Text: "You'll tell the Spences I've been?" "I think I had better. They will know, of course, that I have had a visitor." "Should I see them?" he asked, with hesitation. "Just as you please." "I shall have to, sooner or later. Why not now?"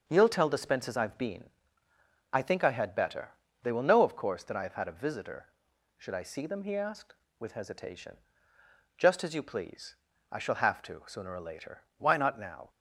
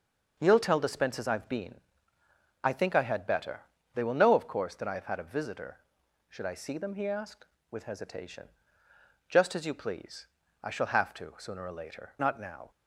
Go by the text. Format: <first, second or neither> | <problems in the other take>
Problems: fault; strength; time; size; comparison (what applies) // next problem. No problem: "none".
first | starts louder than the rest; noticeable; until 1.4 s; 6 dB; noticeable in the first // skips "Why"; at 12.1 s